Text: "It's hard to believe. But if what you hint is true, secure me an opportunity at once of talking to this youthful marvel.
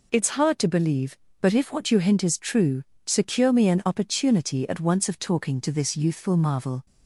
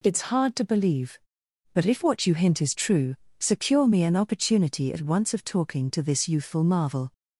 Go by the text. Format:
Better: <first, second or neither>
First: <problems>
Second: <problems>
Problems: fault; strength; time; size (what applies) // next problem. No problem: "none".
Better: neither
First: none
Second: none